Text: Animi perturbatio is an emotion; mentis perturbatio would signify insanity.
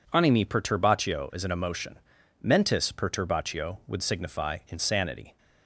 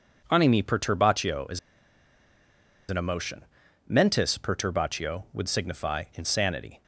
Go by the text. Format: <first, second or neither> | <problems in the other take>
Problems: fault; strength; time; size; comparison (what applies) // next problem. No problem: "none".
first | pauses between "is" and "an"; strong; at 1.5 s; 1.2 s long